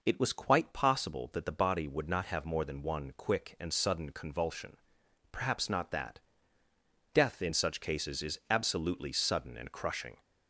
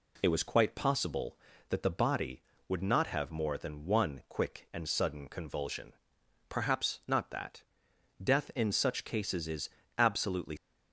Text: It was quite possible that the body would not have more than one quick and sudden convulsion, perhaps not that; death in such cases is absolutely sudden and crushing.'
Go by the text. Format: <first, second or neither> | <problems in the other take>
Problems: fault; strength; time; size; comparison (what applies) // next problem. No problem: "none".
first | pauses between "is" and "absolutely"; slight; at 9.6 s; 0.30 s long // stops before "sudden and crushing"; at 10.5 s